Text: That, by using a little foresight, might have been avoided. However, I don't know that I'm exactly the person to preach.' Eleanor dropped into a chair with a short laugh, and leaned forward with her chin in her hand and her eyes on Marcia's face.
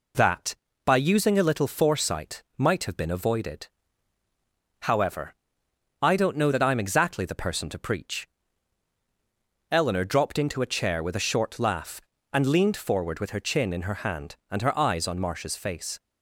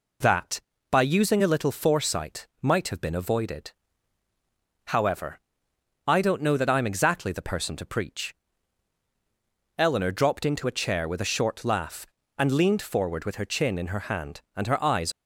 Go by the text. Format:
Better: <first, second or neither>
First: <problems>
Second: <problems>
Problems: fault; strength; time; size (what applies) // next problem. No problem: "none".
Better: first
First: none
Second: stops before "on Marcia's face"; at 15.1 s